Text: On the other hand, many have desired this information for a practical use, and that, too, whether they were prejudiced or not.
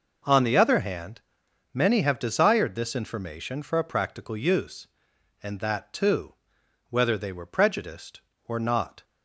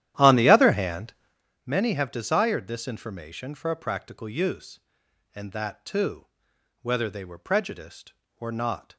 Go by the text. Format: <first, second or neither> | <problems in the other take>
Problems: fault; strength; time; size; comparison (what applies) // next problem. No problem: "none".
first | starts louder than the rest; strong; until 1.4 s; 12 dB